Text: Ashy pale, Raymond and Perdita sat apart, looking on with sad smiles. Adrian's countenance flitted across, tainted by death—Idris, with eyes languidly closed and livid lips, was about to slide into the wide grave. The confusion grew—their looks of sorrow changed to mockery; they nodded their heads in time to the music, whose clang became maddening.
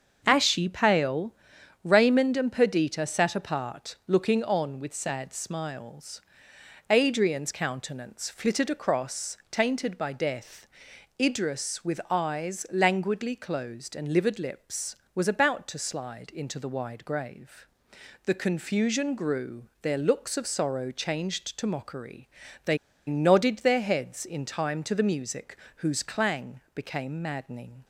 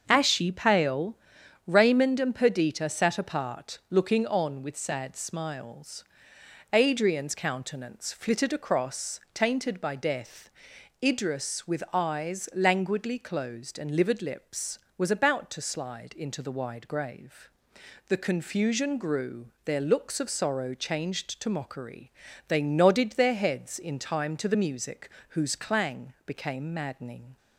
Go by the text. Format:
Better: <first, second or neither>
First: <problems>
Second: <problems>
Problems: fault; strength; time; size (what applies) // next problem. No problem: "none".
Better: second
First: starts louder than the rest; until 1.2 s; 6.5 dB // pauses between "they" and "nodded"; slight; at 22.7 s; 0.31 s long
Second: starts louder than the rest; until 1.0 s; 6.5 dB